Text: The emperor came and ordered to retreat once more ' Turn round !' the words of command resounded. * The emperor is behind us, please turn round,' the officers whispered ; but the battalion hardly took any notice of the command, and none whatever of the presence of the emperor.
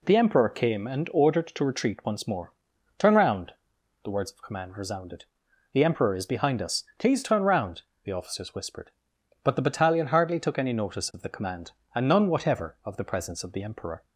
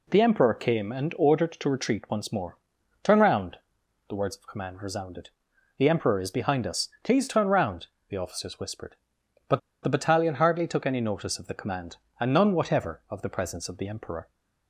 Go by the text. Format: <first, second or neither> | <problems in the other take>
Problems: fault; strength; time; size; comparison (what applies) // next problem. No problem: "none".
first | pauses between "but" and "the"; slight; at 9.5 s; 0.23 s long